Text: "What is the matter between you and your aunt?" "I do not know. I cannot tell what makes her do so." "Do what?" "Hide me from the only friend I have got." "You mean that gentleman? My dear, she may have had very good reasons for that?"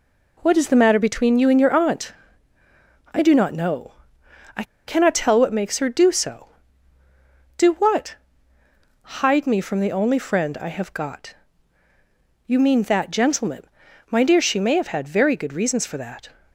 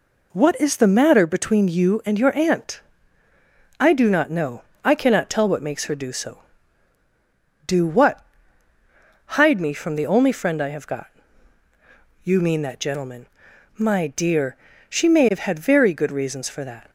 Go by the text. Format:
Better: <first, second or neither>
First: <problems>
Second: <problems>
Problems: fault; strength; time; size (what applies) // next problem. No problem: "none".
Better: second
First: pauses between "I" and "cannot"; slight; at 4.6 s; 0.23 s long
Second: none